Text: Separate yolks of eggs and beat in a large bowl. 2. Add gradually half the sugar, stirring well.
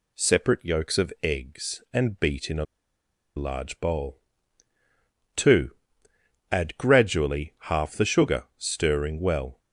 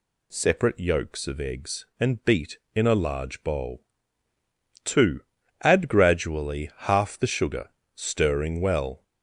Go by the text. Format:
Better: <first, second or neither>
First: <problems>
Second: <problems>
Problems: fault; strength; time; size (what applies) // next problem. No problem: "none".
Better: second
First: pauses between "a" and "large"; noticeable; at 2.6 s; 0.71 s long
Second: none